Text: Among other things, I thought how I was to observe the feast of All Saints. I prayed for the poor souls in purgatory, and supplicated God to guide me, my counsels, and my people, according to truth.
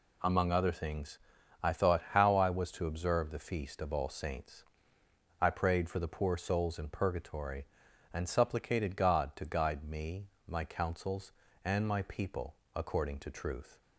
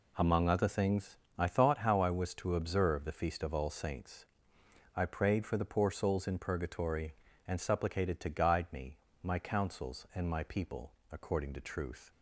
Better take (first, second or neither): first